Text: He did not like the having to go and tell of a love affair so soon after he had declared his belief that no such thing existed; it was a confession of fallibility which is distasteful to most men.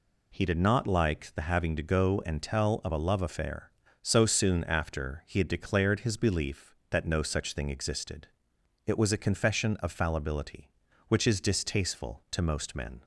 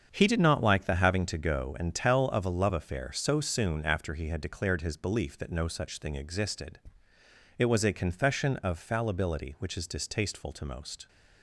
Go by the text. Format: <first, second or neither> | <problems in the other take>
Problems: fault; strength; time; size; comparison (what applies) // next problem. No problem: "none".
first | starts louder than the rest; strong; until 1.1 s; 7.5 dB // stops before "men"; at 11.0 s